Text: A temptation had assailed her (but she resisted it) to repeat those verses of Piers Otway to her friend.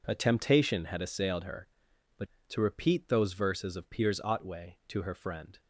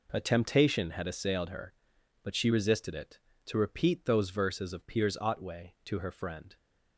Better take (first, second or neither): second